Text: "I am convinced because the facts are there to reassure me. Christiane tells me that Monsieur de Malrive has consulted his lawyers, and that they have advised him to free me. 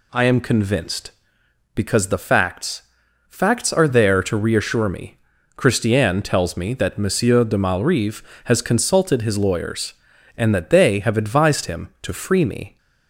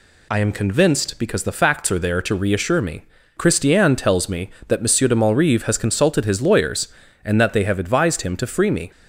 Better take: second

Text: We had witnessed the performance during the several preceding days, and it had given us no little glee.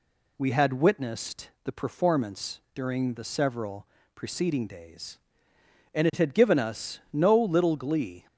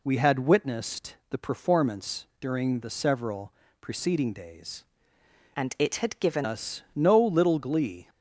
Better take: first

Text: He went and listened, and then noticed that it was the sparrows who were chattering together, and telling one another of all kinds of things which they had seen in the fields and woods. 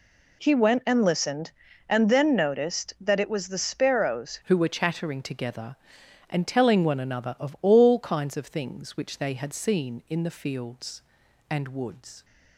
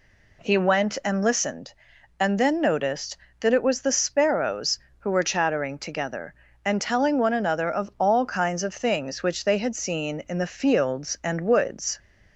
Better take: second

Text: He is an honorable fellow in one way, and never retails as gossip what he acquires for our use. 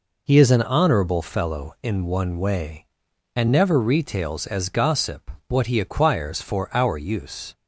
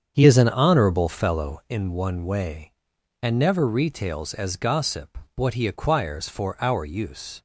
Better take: first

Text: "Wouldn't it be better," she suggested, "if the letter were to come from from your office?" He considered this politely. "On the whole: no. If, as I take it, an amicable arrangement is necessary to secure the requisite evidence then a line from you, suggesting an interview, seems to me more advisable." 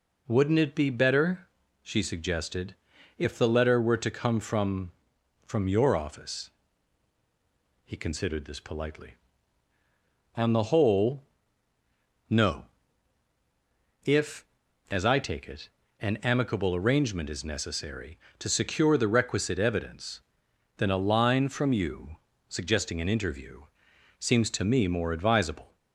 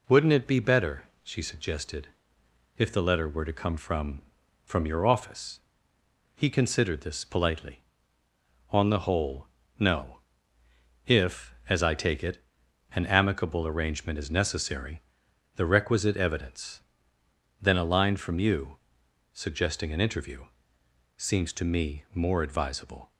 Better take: first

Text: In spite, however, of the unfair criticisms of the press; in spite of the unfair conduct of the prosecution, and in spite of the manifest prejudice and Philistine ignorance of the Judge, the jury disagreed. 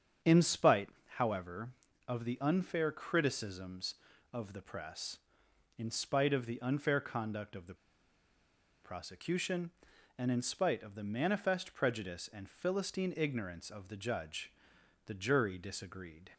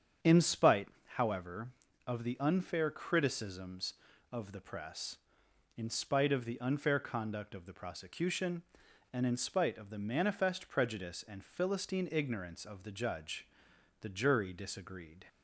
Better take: second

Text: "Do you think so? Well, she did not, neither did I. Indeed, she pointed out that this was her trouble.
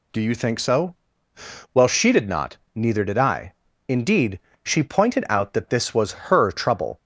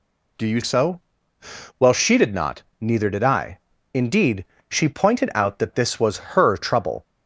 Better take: first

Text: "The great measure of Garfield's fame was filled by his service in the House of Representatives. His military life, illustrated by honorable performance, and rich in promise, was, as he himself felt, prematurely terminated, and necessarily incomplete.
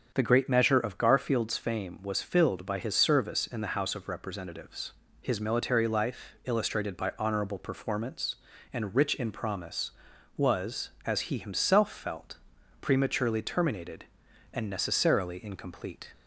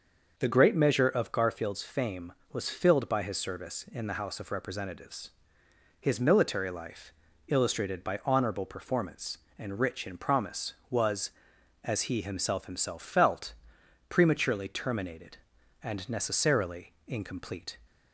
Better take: first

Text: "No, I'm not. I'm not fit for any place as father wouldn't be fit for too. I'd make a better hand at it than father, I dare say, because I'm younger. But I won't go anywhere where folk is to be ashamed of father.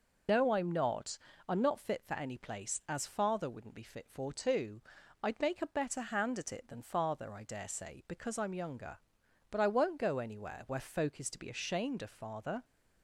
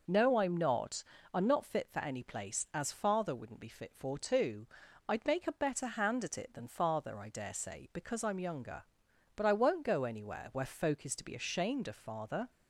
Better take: second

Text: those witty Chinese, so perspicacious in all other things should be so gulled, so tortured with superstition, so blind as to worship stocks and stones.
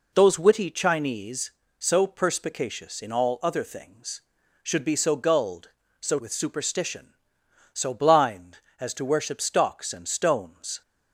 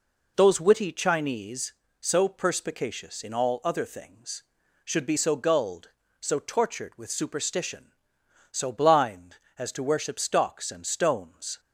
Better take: second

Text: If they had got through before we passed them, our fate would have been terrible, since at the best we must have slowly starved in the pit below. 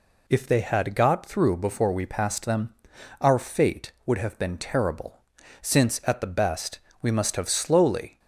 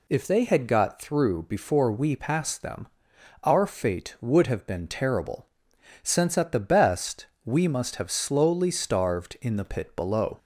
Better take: second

